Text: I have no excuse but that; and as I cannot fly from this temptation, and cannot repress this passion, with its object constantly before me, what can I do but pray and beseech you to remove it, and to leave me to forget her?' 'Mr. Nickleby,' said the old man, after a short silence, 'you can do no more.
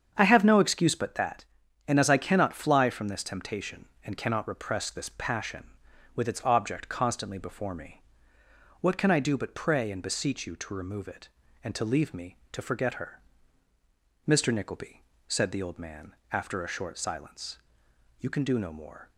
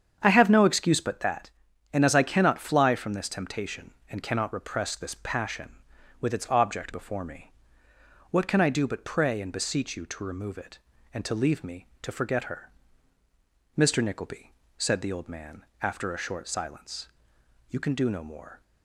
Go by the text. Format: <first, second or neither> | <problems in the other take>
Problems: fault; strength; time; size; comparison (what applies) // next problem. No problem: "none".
first | starts louder than the rest; strong; until 1.2 s; 8 dB; strong in the first // skips "constantly"; at 6.9 s